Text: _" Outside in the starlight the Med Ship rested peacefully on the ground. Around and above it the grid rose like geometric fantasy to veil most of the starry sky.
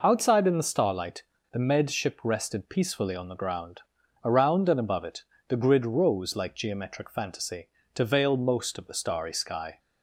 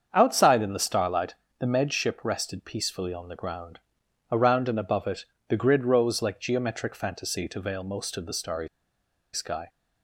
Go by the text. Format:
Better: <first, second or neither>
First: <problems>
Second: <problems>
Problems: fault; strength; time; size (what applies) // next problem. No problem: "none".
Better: first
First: pauses between "starlight" and "the"; slight; at 1.2 s; 0.31 s long // pauses between "it" and "the"; slight; at 5.2 s; 0.26 s long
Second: starts louder than the rest; strong; until 1.1 s; 7 dB // pauses between "starlight" and "the"; slight; at 1.3 s; 0.24 s long // pauses between "it" and "the"; slight; at 5.2 s; 0.24 s long // pauses between "starry" and "sky"; noticeable; at 8.6 s; 0.66 s long